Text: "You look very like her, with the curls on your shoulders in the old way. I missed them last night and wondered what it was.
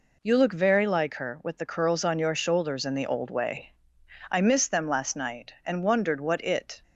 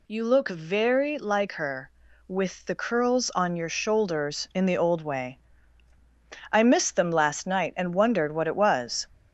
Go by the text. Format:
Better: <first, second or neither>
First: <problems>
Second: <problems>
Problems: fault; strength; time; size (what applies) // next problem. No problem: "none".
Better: second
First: stops before "was"; at 6.8 s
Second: none